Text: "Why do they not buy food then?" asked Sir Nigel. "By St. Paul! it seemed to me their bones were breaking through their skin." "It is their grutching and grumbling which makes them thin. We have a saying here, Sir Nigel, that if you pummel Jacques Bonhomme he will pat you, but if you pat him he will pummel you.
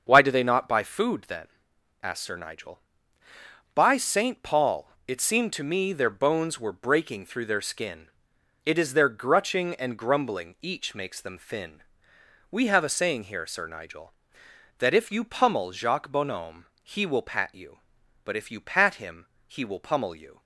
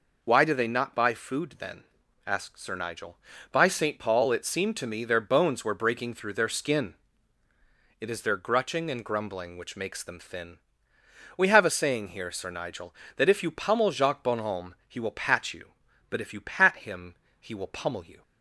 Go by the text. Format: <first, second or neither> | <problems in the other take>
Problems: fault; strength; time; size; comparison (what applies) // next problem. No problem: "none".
second | starts louder than the rest; until 1.0 s; 6.5 dB // says "each" for "which"; at 10.6 s // pauses between "Bonhomme" and "he"; slight; at 16.6 s; 0.16 s long // pauses between "him" and "he"; slight; at 19.2 s; 0.20 s long; slight in the second